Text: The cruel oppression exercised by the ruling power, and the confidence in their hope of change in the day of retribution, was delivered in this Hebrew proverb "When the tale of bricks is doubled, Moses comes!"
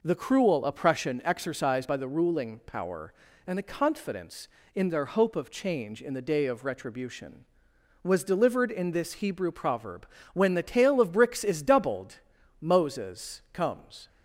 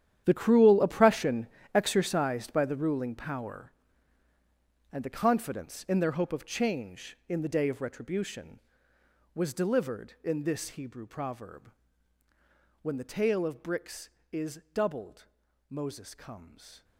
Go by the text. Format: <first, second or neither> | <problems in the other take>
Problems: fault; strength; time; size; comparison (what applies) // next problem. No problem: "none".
first | gets quieter; strong; throughout; 15.5 dB // pauses between "oppression" and "exercised"; slight; at 1.4 s; 0.28 s long // pauses between "proverb" and "When"; at 11.6 s; 1.1 s long; slight in the first